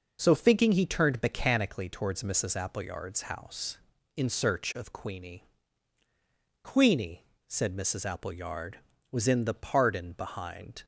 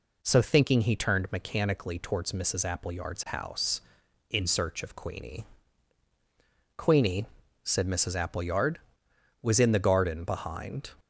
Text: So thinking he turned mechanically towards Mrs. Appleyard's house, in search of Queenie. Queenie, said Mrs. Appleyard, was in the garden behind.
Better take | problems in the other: second | says "pardon" for "garden"; at 9.5 s

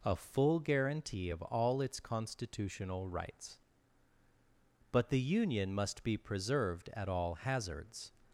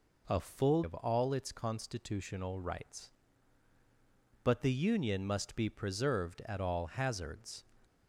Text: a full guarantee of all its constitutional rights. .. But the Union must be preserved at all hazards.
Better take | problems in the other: first | skips "guarantee"; at 0.8 s

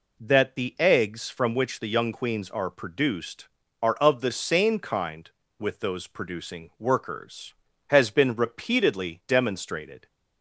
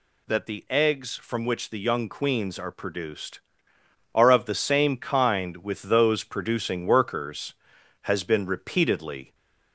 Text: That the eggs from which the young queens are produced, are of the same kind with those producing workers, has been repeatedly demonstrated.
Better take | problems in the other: first | stops before "demonstrated"; at 9.3 s

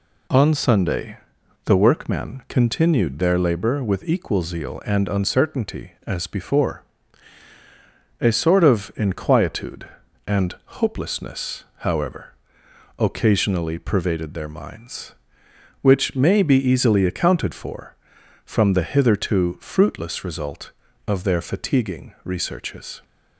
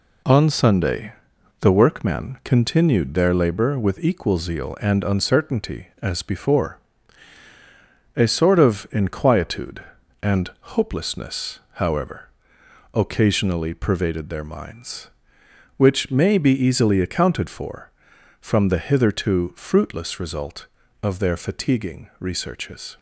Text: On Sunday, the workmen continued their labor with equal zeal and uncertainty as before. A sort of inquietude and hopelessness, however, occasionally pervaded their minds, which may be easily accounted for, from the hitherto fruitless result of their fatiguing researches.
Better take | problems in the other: first | gets quieter; throughout; 6.5 dB

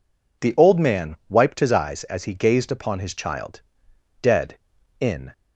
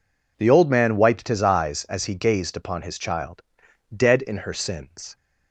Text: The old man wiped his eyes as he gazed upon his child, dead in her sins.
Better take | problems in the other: second | stops before "her sins"; at 5.3 s

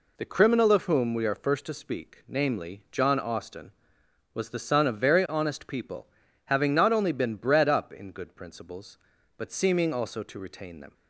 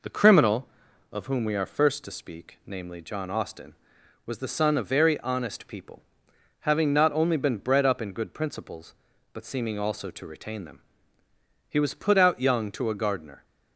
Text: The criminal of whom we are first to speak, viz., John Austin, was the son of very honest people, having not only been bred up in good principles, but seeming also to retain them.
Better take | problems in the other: first | goes on to say "He was put out young to a gardener"; strong; from 11.6 s on; 1.7 s long

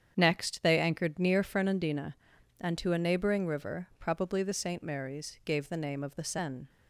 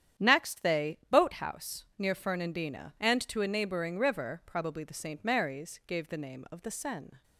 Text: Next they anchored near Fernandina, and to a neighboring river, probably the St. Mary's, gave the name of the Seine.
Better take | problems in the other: first | starts louder than the rest; strong; until 1.3 s; 9.5 dB; strong in the first // says "boathouse" for "anchored"; at 1.1 s

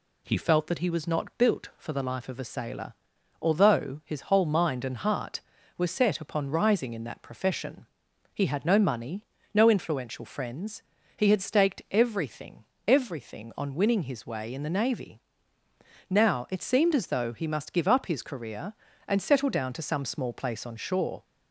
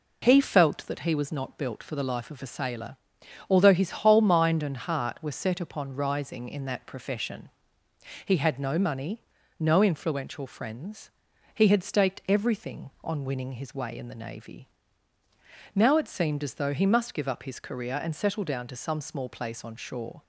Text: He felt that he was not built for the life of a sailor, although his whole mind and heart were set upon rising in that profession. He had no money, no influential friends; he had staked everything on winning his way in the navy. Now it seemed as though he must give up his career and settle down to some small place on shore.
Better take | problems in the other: second | says "everything" twice; at 12.8 s

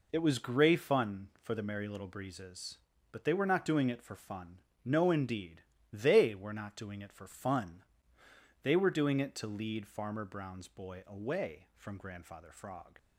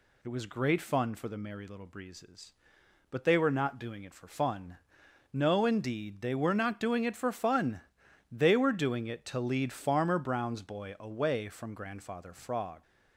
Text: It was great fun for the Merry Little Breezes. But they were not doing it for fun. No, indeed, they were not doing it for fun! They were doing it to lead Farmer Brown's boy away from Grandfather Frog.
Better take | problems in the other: second | says "grey" for "great"; at 0.3 s

